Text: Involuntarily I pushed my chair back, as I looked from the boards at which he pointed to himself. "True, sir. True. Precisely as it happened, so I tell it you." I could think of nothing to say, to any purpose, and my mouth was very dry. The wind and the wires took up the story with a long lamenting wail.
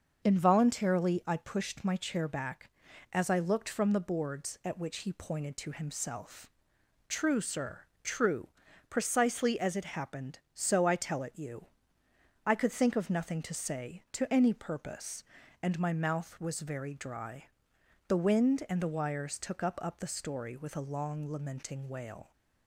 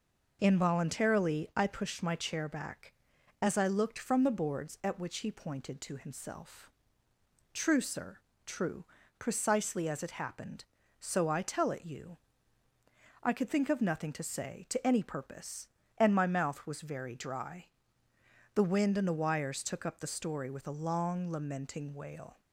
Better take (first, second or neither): second